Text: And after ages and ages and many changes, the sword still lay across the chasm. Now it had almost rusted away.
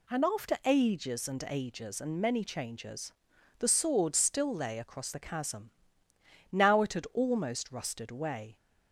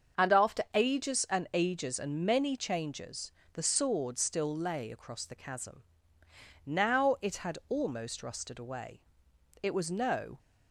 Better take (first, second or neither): first